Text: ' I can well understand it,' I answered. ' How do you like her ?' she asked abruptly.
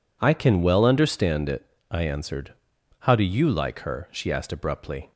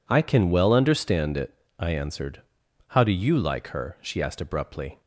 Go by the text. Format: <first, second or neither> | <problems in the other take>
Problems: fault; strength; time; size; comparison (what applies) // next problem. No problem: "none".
neither | none